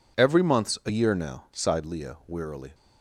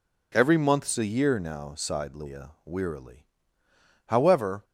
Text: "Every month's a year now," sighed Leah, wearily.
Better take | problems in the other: first | goes on to say "However"; from 4.0 s on; 0.58 s long

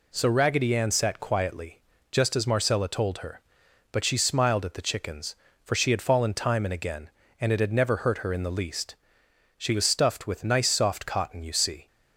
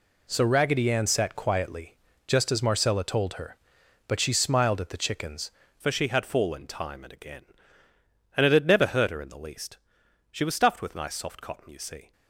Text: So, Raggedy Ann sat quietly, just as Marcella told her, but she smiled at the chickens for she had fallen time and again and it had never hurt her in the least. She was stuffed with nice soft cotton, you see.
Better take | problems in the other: first | changes voice at "for"; from 5.8 s on; 6.3 s long

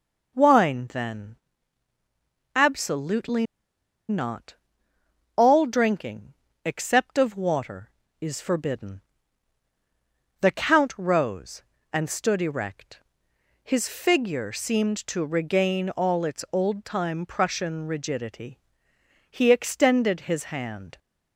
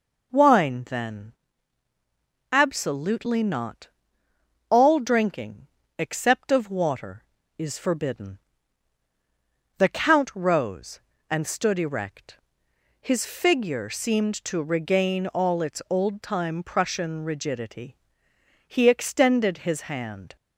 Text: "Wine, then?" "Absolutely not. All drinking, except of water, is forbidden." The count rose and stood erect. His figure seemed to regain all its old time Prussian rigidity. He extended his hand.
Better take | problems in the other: second | pauses between "Absolutely" and "not"; noticeable; at 3.4 s; 0.64 s long

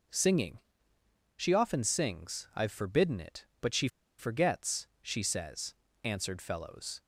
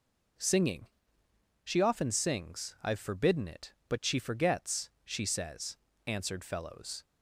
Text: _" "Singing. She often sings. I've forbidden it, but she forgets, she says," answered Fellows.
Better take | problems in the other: second | pauses between "she" and "forgets"; slight; at 3.8 s; 0.31 s long

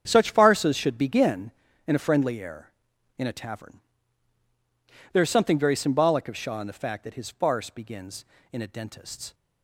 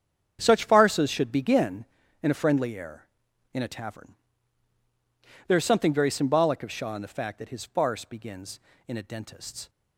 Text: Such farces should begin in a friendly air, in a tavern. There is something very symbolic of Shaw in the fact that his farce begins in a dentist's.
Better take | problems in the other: neither | starts louder than the rest; strong; the same in both

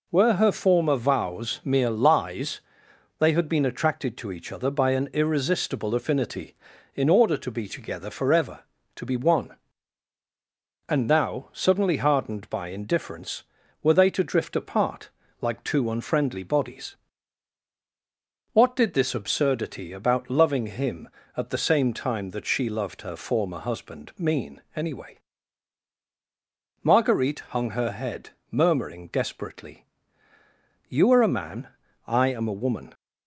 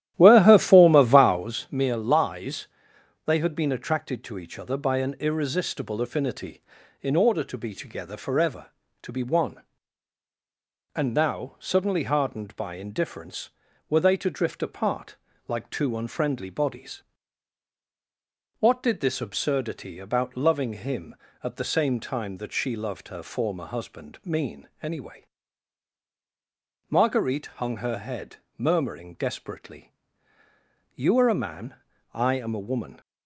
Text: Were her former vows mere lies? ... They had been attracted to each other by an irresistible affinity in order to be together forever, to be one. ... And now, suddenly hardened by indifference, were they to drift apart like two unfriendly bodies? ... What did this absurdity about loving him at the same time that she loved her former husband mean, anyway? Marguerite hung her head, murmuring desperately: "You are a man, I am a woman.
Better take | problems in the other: first | starts louder than the rest; strong; until 1.6 s; 12.5 dB // pauses between "apart" and "like"; slight; at 15.1 s; 0.32 s long; slight in the first

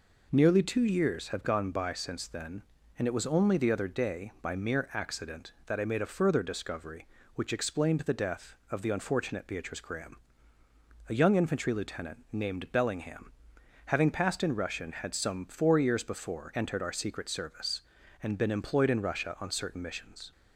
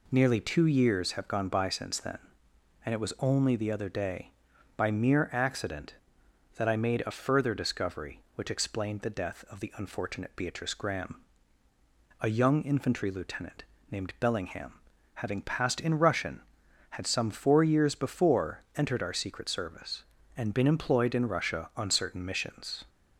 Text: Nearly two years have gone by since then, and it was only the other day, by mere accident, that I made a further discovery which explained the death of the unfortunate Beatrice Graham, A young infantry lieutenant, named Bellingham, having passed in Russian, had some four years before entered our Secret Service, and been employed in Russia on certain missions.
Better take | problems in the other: neither | none

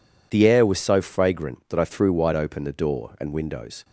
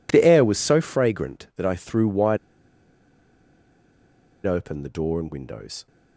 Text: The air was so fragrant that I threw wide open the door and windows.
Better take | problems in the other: first | pauses between "wide" and "open"; strong; at 2.3 s; 2.0 s long

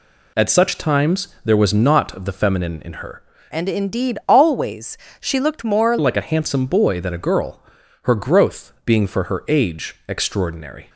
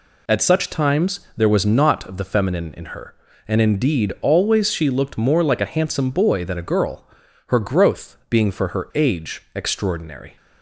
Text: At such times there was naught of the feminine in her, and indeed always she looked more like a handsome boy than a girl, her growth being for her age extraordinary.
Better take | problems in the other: second | pauses between "times" and "there"; slight; at 1.2 s; 0.16 s long; slight in the second // changes voice from "and" to "more"; from 3.5 to 5.9 s; 2.4 s long // pauses between "always" and "she"; slight; at 4.9 s; 0.22 s long

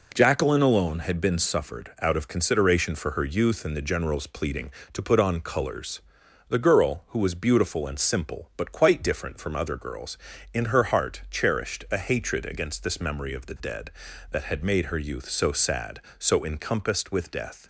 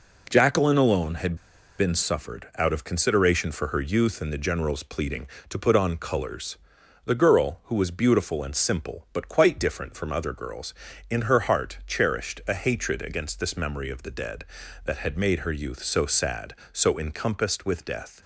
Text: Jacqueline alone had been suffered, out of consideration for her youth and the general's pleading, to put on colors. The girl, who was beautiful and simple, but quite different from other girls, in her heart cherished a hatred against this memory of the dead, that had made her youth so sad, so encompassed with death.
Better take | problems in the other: first | pauses between "had" and "been"; at 1.3 s; 0.40 s long

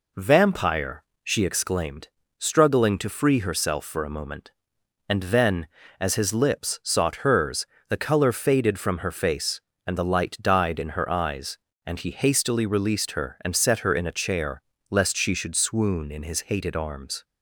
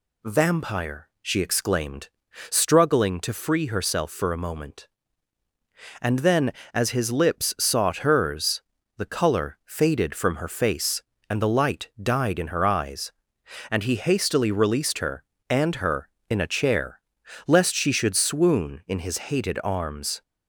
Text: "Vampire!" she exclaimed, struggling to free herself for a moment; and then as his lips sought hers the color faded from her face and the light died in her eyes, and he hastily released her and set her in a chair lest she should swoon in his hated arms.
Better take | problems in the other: first | pauses between "hers" and "the"; slight; at 8.6 s; 0.36 s long; slight in the first // skips "set"; at 15.7 s // pauses between "chair" and "lest"; noticeable; at 16.9 s; 0.48 s long; slight in the first

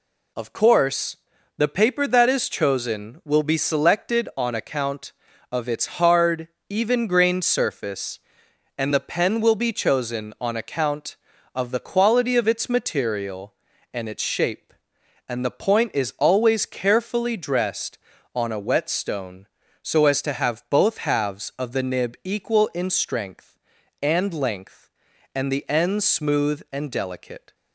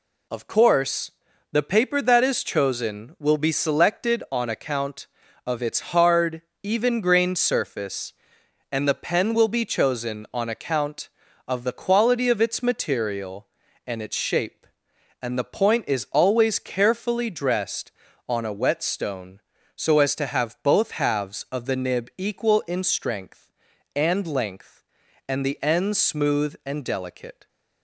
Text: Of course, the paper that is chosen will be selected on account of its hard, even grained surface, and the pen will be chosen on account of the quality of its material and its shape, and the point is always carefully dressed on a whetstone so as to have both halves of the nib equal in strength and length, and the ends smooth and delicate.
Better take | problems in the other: neither | none

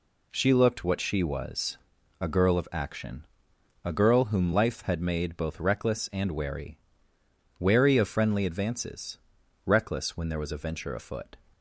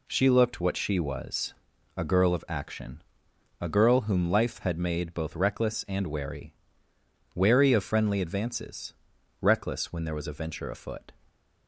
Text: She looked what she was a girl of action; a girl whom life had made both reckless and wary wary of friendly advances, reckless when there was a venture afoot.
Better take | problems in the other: neither | pauses between "was" and "a"; the same in both // pauses between "wary" and "wary"; noticeable; the same in both

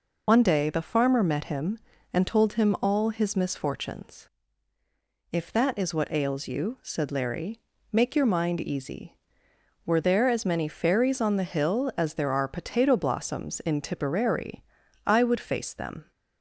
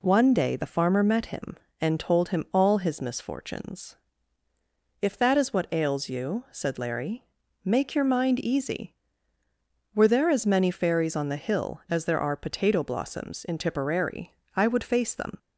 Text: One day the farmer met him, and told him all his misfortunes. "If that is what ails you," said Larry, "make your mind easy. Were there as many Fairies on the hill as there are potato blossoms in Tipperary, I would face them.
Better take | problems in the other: second | loses the start of "One"; at 0.2 s; 55 ms

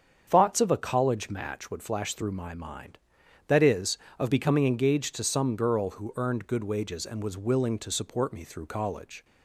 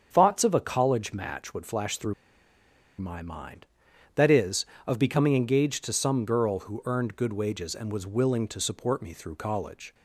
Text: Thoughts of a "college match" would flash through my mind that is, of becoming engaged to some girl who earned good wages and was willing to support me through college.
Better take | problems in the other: first | starts louder than the rest; strong; until 1.1 s; 7.5 dB; strong in the first // pauses between "through" and "my"; noticeable; at 2.1 s; 0.86 s long

